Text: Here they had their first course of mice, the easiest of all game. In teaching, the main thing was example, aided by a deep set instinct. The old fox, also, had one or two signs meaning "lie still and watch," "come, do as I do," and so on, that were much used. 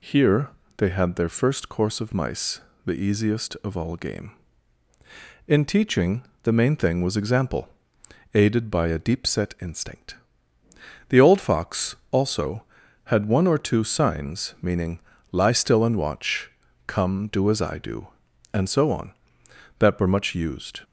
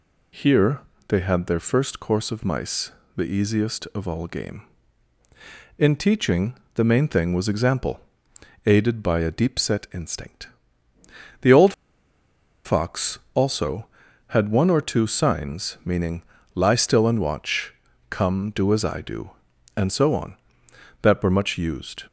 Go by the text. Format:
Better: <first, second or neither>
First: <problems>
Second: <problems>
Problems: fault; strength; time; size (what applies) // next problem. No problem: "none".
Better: first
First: pauses between "Here" and "they"; slight; at 0.4 s; 0.30 s long // pauses between "meaning" and "lie"; slight; at 14.9 s; 0.32 s long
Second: pauses between "Here" and "they"; slight; at 0.7 s; 0.30 s long // pauses between "old" and "fox"; noticeable; at 11.7 s; 0.93 s long // pauses between "meaning" and "lie"; slight; at 16.2 s; 0.32 s long